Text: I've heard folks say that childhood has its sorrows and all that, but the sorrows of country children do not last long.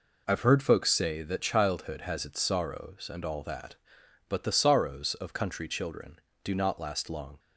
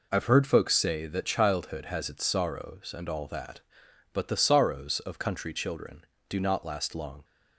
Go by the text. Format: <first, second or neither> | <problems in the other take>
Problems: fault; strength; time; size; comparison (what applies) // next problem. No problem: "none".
neither | none